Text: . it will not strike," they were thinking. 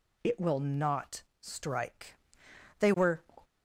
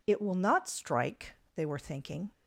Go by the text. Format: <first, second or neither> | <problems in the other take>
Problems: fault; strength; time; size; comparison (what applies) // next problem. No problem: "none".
second | pauses between "not" and "strike"; slight; at 1.2 s; 0.18 s long // stops before "thinking"; at 3.4 s